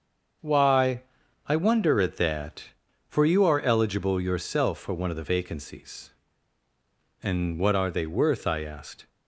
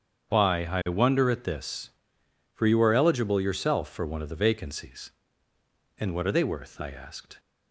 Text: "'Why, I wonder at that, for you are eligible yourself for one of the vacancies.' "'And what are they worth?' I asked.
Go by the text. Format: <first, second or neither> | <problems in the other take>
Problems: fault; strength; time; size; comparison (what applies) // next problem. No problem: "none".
first | starts louder than the rest; strong; until 1.3 s; 7.5 dB; also in the first // says "this" for "that"; at 1.4 s